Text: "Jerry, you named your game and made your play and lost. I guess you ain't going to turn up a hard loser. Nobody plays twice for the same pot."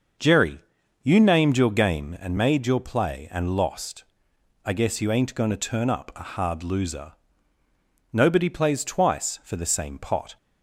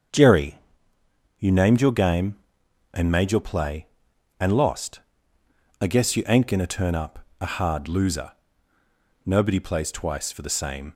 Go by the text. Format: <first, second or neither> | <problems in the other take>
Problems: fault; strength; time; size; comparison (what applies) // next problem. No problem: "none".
first | starts louder than the rest; until 1.9 s; 6.5 dB; noticeable in the first // pauses between "up" and "a"; slight; at 7.1 s; 0.20 s long // stops before "pot"; at 10.9 s